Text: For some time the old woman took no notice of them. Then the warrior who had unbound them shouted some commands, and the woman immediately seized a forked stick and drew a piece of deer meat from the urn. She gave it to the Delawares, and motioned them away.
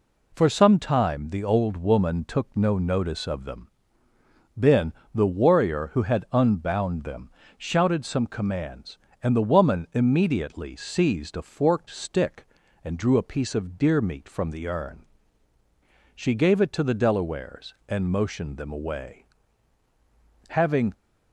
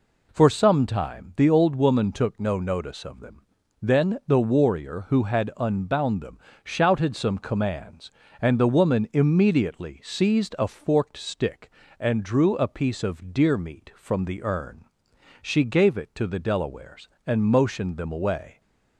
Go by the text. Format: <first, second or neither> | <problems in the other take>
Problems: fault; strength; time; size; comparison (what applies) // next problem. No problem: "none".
second | pauses between "Then" and "the"; slight; at 4.9 s; 0.22 s long // pauses between "them" and "shouted"; slight; at 7.2 s; 0.28 s long; slight in the second // goes on to say "Having"; slight; from 20.4 s on; 0.44 s long